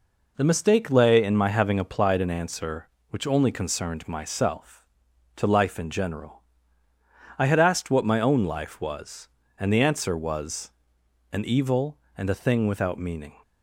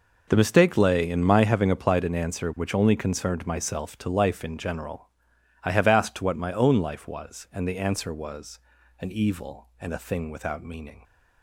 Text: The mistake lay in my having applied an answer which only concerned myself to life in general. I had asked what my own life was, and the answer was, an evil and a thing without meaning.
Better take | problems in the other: first | says "have" for "had"; at 5.7 s

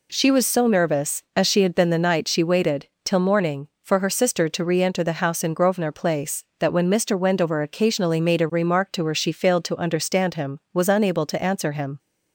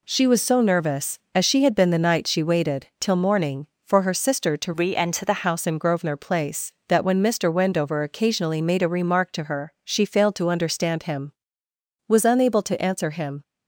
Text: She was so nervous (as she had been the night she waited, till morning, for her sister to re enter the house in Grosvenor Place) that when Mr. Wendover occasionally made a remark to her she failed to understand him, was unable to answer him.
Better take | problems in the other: first | changes voice from "re" to "the"; from 4.7 to 5.4 s; 0.7 s long

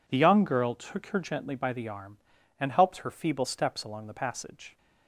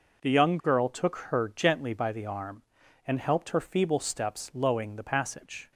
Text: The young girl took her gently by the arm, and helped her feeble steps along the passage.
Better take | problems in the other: first | says "lowing" for "along"; at 4.5 s

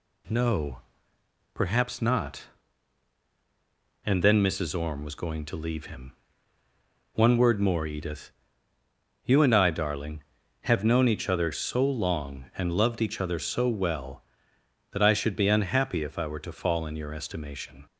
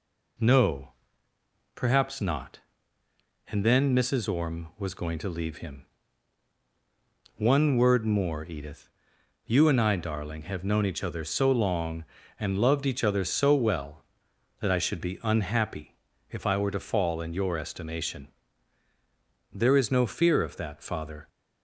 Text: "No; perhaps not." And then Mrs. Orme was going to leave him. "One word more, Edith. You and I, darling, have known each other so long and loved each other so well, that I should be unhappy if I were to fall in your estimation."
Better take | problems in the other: first | pauses between "unhappy" and "if"; slight; at 15.9 s; 0.34 s long // goes on to say "There is no fear of that father"; strong; from 19.5 s on; 1.7 s long

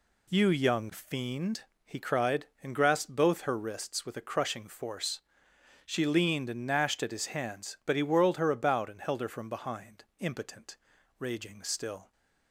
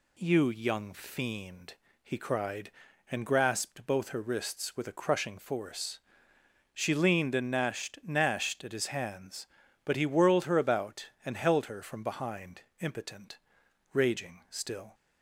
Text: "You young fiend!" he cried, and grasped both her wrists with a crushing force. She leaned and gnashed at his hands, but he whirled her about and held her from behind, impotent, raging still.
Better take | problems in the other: first | says "gnashed" twice; at 8.0 s

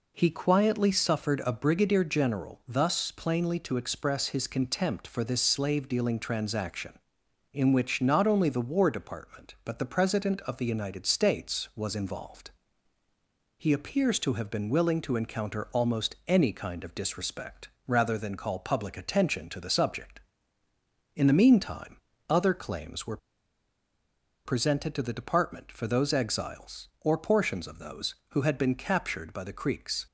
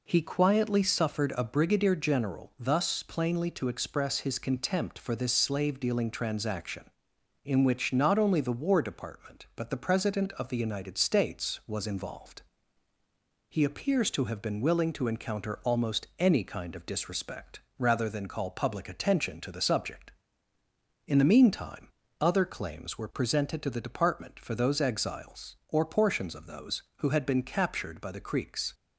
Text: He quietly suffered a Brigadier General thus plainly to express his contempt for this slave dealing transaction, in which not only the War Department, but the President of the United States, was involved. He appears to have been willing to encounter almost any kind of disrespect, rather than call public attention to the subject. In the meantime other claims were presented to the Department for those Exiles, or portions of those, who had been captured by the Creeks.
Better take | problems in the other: second | pauses between "meantime" and "other"; slight; at 21.9 s; 0.32 s long; slight in the second // pauses between "were" and "presented"; strong; at 23.1 s; 1.2 s long

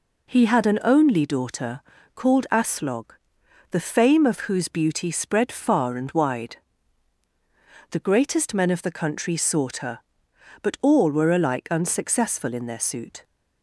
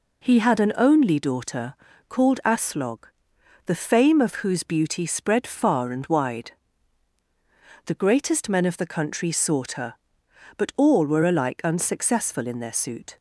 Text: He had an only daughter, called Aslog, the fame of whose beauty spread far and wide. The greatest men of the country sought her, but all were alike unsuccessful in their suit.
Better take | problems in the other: neither | none

